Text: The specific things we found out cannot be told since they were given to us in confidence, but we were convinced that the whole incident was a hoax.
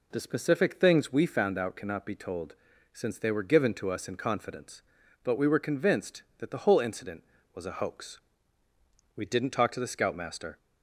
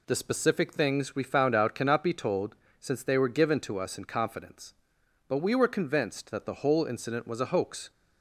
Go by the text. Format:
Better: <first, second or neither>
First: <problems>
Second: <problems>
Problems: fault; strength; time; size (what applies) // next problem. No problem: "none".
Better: second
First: pauses between "told" and "since"; at 2.5 s; 0.38 s long // goes on to say "We didn't talk to the scoutmaster"; from 9.1 s on; 1.4 s long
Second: pauses between "told" and "since"; slight; at 2.5 s; 0.24 s long